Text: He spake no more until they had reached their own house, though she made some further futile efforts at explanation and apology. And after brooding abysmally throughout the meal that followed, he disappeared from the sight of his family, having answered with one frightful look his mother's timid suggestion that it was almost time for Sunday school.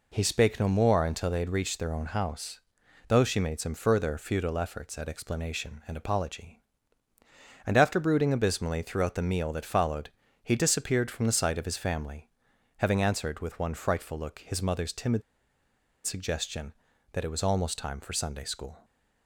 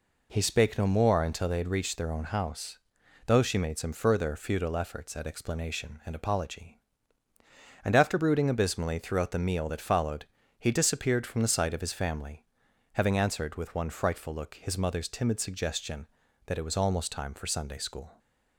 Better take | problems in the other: second | pauses between "timid" and "suggestion"; noticeable; at 15.2 s; 0.84 s long

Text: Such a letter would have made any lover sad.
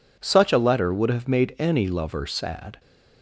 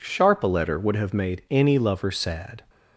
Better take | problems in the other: first | says "Sharp" for "Such"; at 0.0 s

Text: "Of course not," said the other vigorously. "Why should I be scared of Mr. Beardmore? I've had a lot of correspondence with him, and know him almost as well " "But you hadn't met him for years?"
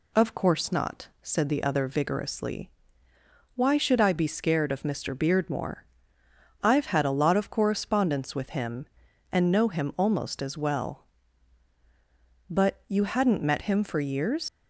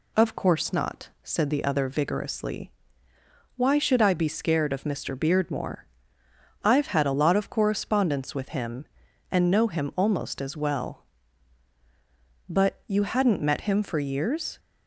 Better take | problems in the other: second | leaves "years" unfinished; at 14.4 s; 110 ms

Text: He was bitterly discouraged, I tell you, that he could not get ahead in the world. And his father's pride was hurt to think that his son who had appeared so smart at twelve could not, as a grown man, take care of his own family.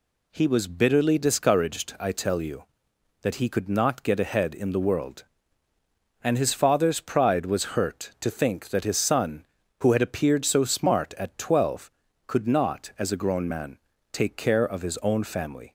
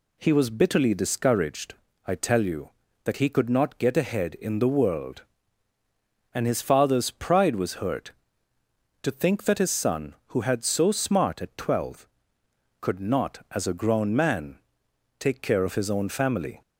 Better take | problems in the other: first | skips "appeared"; at 10.6 s

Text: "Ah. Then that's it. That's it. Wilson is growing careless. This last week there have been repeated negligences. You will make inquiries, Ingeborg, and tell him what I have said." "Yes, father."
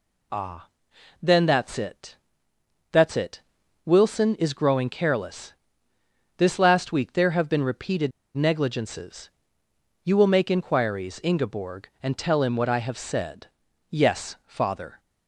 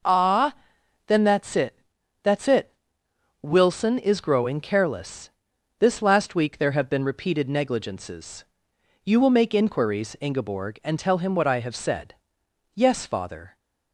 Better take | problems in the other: second | pauses between "repeated" and "negligences"; slight; at 8.1 s; 0.26 s long

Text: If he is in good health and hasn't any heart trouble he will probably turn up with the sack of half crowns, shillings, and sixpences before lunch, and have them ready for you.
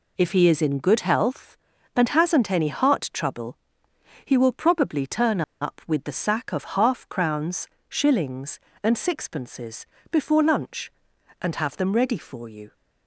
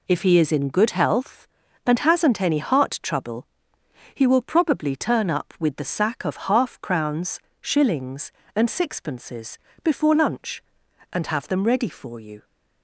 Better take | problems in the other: second | pauses between "trouble" and "he"; noticeable; at 3.5 s; 0.66 s long; noticeable in the second // pauses between "turn" and "up"; slight; at 5.4 s; 0.19 s long // pauses between "sixpences" and "before"; slight; at 9.8 s; 0.26 s long; slight in the second

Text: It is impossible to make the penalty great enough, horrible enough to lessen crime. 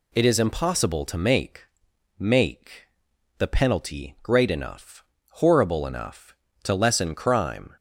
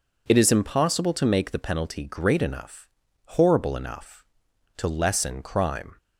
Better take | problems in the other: second | says "make" twice; at 2.1 s

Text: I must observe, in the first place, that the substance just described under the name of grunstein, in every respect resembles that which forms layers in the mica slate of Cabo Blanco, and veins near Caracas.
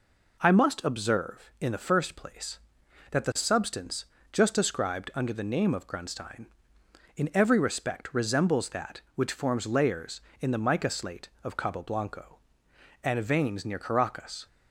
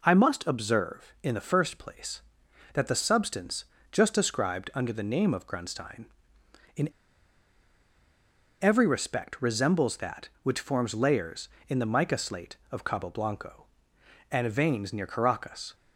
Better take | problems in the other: first | pauses between "substance" and "just"; slight; at 3.6 s; 0.28 s long; slight in the first // pauses between "in" and "every"; strong; at 6.8 s; 1.7 s long

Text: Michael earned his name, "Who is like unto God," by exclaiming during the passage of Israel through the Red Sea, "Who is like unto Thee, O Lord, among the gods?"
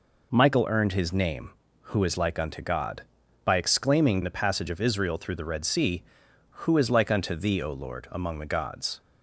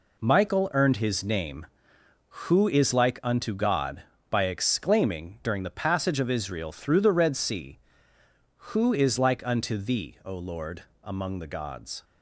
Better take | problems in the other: second | skips "during"; at 4.2 s

